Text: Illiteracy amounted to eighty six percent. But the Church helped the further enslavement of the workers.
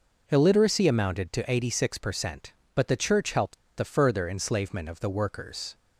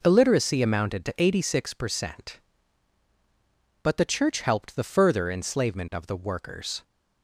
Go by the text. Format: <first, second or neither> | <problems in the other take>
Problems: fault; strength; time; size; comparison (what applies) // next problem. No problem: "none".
second | pauses between "helped" and "the"; slight; at 3.5 s; 0.19 s long